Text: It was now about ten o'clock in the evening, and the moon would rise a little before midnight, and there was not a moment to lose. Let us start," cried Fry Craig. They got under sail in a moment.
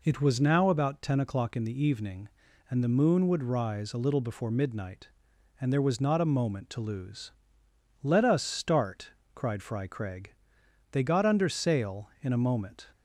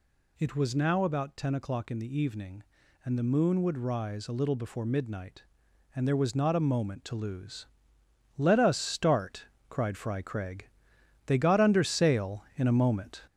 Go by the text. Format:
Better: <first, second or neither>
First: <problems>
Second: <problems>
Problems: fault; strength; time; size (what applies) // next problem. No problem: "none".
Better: first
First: none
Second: gets louder; noticeable; throughout; 4 dB